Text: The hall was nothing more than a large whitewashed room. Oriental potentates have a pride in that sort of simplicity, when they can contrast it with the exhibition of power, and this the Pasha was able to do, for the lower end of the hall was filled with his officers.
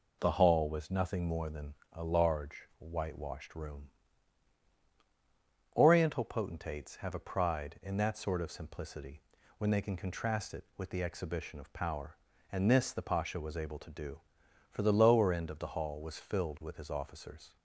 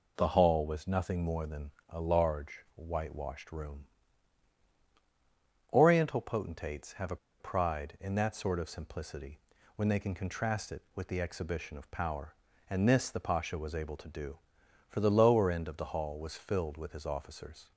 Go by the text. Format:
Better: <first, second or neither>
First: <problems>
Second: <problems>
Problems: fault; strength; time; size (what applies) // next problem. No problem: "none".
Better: first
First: pauses between "than" and "a"; slight; at 1.7 s; 0.20 s long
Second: pauses between "than" and "a"; slight; at 1.7 s; 0.20 s long // pauses between "a" and "pride"; slight; at 7.1 s; 0.23 s long